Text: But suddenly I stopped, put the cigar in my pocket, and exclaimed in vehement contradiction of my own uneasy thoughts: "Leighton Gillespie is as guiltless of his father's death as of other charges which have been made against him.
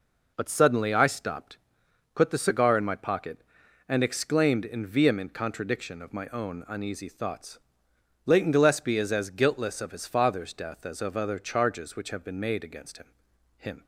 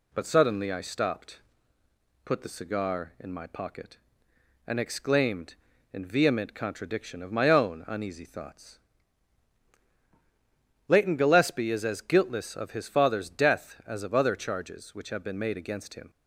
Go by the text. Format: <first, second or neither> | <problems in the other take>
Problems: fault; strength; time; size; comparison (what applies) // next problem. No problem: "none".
second | says "him" twice; at 13.5 s